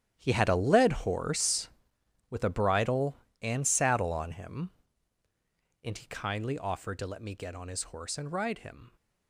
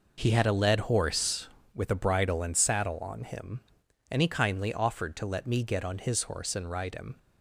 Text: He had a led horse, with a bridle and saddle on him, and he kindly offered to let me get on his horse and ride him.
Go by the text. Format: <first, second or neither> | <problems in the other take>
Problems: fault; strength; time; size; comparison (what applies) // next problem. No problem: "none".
second | gets quieter; strong; throughout; 14.5 dB